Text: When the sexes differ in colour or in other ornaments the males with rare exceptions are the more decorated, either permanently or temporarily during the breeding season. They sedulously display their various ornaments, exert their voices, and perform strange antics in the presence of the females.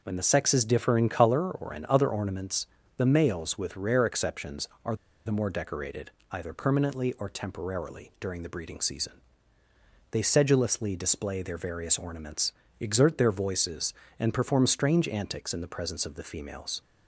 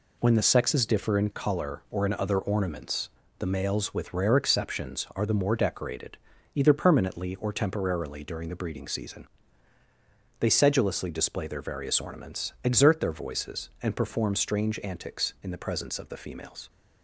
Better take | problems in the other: second | pauses between "ornaments" and "the"; slight; at 2.6 s; 0.30 s long; slight in the second // pauses between "are" and "the"; slight; at 4.9 s; 0.29 s long

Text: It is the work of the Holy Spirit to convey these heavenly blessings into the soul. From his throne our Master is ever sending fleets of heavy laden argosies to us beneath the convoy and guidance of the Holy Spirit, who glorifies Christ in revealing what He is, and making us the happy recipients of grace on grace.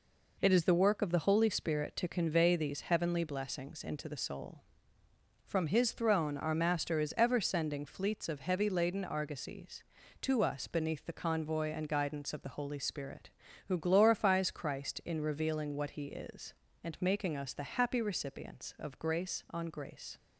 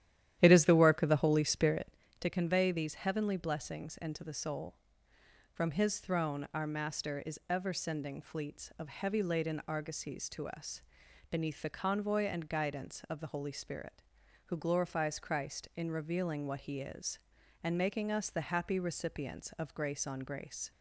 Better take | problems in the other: first | starts louder than the rest; strong; until 2.0 s; 11.5 dB // pauses between "us" and "beneath"; noticeable; at 10.8 s; 0.48 s long

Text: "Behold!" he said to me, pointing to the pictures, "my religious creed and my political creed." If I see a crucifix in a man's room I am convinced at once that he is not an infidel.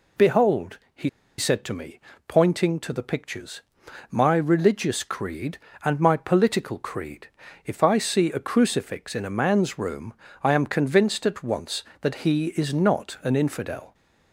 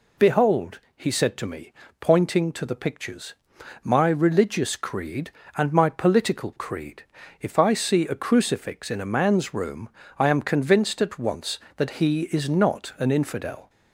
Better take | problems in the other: second | pauses between "he" and "said"; slight; at 1.0 s; 0.30 s long // pauses between "room" and "I"; slight; at 10.1 s; 0.30 s long; slight in the second

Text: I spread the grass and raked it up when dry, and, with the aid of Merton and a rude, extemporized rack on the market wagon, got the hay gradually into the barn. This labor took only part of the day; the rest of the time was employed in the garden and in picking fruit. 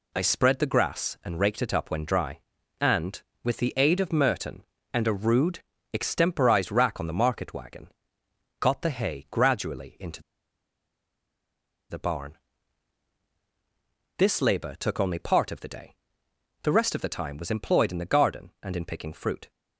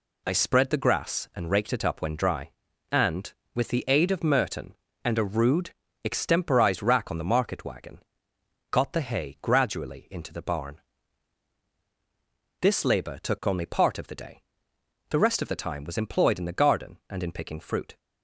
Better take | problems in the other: second | pauses between "into" and "the"; strong; at 10.2 s; 1.6 s long

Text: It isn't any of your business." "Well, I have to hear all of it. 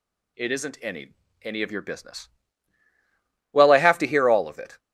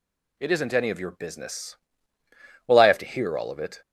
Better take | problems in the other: second | says "any" twice; at 1.4 s

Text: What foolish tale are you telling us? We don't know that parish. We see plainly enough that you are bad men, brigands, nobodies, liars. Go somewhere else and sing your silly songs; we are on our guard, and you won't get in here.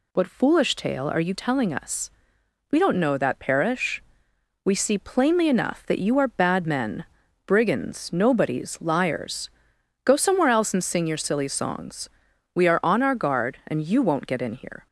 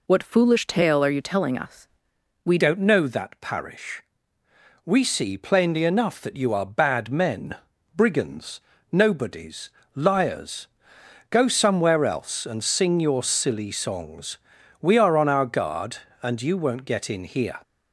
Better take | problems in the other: first | changes voice at "don't"; from 2.6 s on; 15.0 s long

